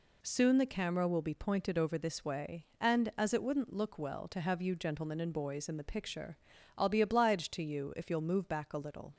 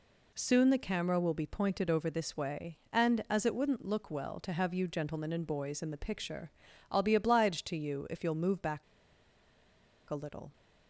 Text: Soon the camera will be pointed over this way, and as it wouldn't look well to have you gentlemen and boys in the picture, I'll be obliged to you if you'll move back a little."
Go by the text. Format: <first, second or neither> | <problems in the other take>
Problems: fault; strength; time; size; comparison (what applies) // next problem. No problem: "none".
first | pauses between "back" and "a"; strong; at 8.8 s; 1.2 s long